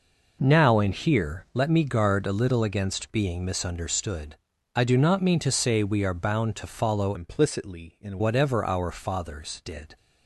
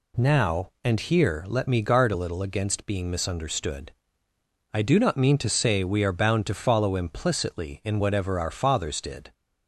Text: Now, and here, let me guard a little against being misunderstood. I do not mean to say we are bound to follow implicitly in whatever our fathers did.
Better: second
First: changes voice from "implicitly" to "in"; from 7.1 to 8.2 s; 1.1 s long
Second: none

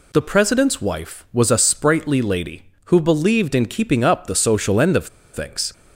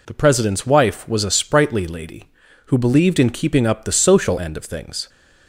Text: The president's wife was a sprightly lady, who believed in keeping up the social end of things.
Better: second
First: pauses between "of" and "things"; slight; at 5.0 s; 0.27 s long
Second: none

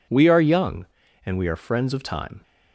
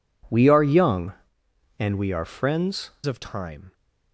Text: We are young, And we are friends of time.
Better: first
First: none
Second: changes voice at "of"; from 3.0 s on; 0.7 s long

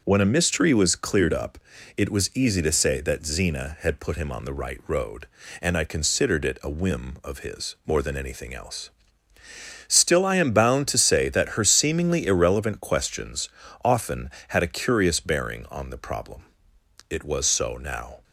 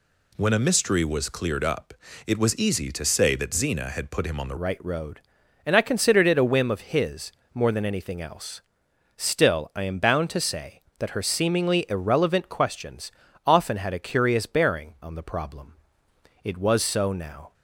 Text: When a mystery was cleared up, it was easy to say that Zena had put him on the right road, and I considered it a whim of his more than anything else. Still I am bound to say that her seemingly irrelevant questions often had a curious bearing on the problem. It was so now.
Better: first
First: pauses between "questions" and "often"; slight; at 13.4 s; 0.36 s long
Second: changes voice at "right"; from 4.5 s on; 13.0 s long // pauses between "his" and "more"; slight; at 7.3 s; 0.24 s long // pauses between "questions" and "often"; slight; at 13.1 s; 0.36 s long

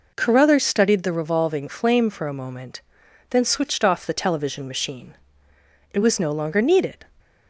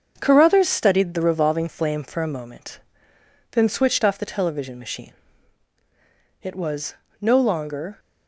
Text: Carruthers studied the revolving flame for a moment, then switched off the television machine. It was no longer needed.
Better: first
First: none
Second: starts louder than the rest; until 1.1 s; 6.5 dB // pauses between "was" and "no"; slight; at 6.9 s; 0.26 s long // stops before "needed"; at 7.9 s

